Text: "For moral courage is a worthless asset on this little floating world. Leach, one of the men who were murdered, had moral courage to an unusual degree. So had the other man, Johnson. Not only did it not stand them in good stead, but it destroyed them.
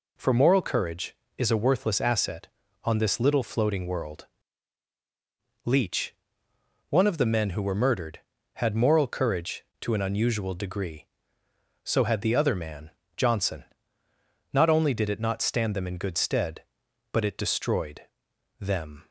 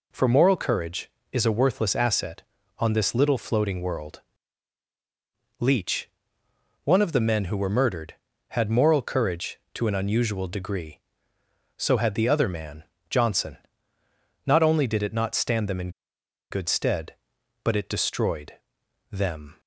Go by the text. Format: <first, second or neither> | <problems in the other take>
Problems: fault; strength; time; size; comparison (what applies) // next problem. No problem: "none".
first | pauses between "in" and "good"; noticeable; at 15.8 s; 0.61 s long // pauses between "destroyed" and "them"; noticeable; at 18.5 s; 0.56 s long; noticeable in the first